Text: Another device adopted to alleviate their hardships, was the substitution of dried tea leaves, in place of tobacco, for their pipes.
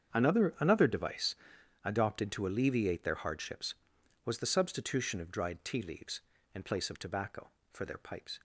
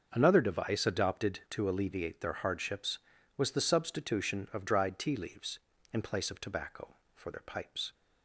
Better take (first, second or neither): second